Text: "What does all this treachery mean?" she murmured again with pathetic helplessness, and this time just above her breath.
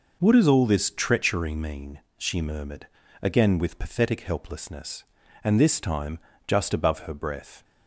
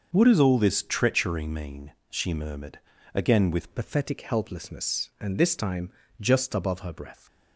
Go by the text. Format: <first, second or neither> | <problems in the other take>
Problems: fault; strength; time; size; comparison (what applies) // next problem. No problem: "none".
first | pauses between "murmured" and "again"; slight; at 2.8 s; 0.34 s long; slight in the first // changes voice at "pathetic"; from 3.7 s on; 3.5 s long // pauses between "time" and "just"; slight; at 5.8 s; 0.30 s long; slight in the first